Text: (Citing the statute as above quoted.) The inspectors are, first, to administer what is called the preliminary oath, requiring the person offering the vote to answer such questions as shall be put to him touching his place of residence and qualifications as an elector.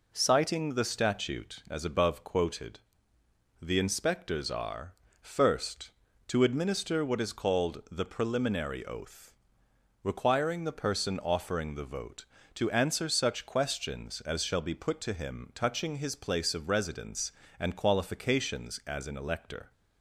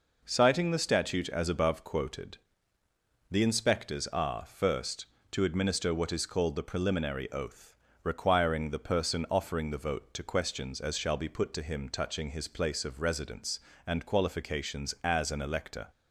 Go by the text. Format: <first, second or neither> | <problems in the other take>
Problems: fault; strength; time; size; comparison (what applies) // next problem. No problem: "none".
first | skips "answer such"; at 10.2 s